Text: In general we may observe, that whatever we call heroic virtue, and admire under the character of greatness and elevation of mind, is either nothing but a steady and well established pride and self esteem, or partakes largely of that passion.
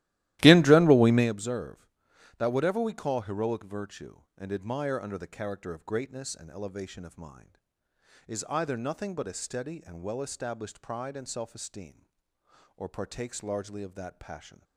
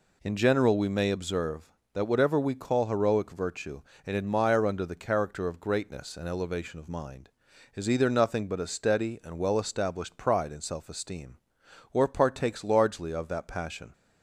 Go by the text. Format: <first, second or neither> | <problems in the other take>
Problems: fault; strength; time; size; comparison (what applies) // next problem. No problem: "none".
second | starts louder than the rest; strong; until 1.3 s; 15.5 dB